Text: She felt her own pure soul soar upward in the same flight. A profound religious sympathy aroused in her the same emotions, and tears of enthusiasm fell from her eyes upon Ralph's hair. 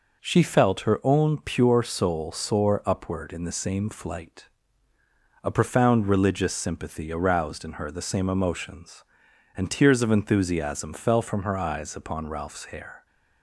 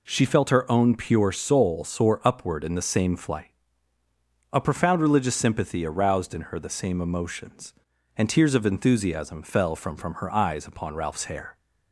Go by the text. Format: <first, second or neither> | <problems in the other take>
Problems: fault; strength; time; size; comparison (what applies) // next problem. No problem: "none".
first | says "from" twice; at 9.9 s